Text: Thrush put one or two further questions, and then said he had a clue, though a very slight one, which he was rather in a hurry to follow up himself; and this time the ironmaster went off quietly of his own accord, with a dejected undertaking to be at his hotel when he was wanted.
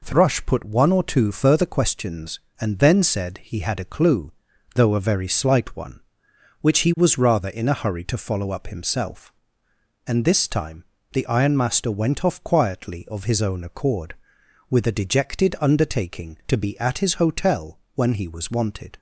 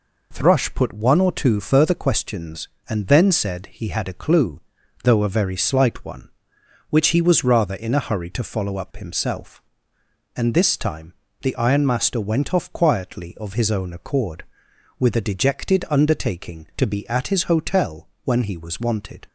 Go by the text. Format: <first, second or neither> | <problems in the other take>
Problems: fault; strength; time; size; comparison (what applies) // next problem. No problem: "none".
neither | pauses between "time" and "the"; slight; the same in both // pauses between "hotel" and "when"; slight; the same in both